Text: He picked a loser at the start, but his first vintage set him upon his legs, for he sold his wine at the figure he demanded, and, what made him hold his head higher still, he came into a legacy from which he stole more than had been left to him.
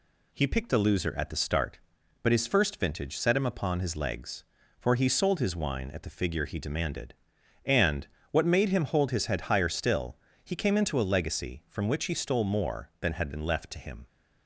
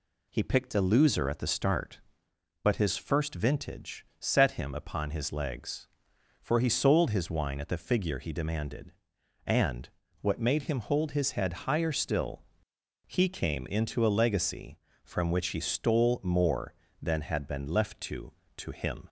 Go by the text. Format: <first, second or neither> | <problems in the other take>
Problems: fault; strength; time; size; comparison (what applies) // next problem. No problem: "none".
first | pauses between "vintage" and "set"; slight; at 4.0 s; 0.16 s long // says "to" twice; at 18.5 s